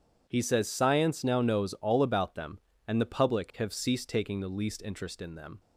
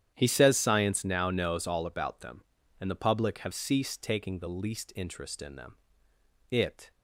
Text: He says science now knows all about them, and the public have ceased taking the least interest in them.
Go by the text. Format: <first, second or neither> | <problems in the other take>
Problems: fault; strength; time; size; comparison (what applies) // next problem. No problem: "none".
first | starts louder than the rest; strong; until 1.1 s; 10 dB // goes on to say "It"; slight; from 6.5 s on; 0.40 s long